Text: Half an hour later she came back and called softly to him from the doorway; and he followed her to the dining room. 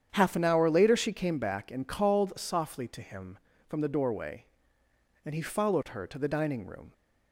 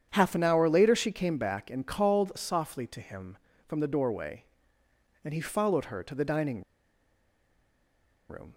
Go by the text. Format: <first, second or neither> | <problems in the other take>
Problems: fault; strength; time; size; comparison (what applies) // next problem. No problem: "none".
first | starts louder than the rest; strong; until 1.1 s; 8.5 dB; strong in the first // pauses between "dining" and "room"; strong; at 6.6 s; 1.6 s long